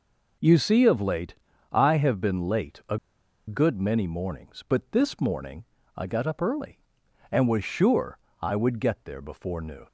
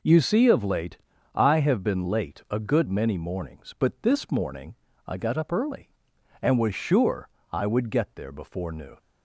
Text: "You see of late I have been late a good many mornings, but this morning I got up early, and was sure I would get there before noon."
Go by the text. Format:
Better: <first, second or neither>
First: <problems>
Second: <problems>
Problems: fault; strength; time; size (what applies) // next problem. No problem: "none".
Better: second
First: pauses between "late" and "I"; at 1.3 s; 0.38 s long // pauses between "a" and "good"; noticeable; at 2.9 s; 0.51 s long // pauses between "morning" and "I"; slight; at 5.6 s; 0.32 s long // pauses between "sure" and "I"; slight; at 8.1 s; 0.24 s long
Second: pauses between "late" and "I"; at 0.9 s; 0.38 s long // pauses between "morning" and "I"; slight; at 4.7 s; 0.32 s long // pauses between "sure" and "I"; slight; at 7.2 s; 0.24 s long